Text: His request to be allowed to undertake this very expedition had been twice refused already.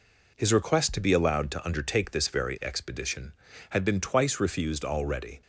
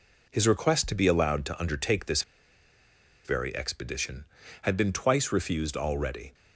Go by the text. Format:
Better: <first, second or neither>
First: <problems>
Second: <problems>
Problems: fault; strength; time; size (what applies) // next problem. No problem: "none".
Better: first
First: none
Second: pauses between "this" and "very"; at 2.2 s; 1.0 s long